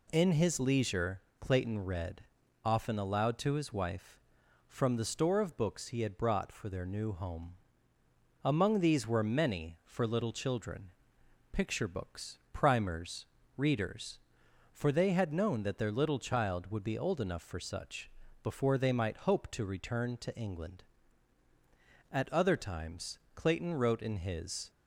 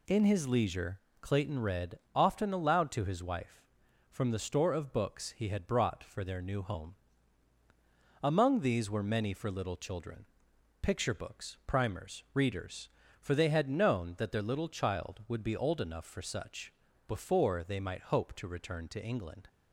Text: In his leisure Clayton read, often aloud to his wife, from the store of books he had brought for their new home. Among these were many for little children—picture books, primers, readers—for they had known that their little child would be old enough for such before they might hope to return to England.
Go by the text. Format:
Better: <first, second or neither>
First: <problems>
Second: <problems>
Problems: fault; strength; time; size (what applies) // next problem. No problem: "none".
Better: second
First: pauses between "leisure" and "Clayton"; slight; at 1.1 s; 0.20 s long // pauses between "such" and "before"; slight; at 18.0 s; 0.34 s long // goes on to say "At other times Clayton wrote in his"; strong; from 22.0 s on; 2.6 s long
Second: pauses between "leisure" and "Clayton"; slight; at 0.9 s; 0.22 s long // pauses between "such" and "before"; slight; at 16.7 s; 0.36 s long